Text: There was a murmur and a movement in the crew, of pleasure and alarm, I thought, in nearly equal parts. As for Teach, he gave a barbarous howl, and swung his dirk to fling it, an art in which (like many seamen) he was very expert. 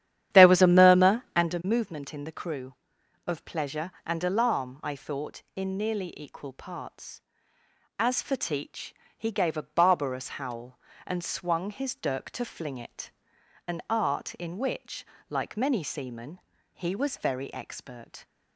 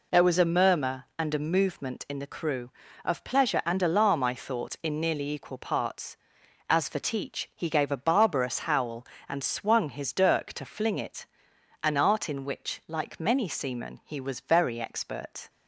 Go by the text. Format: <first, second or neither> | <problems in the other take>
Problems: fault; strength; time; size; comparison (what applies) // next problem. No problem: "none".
second | starts louder than the rest; strong; until 1.5 s; 10.5 dB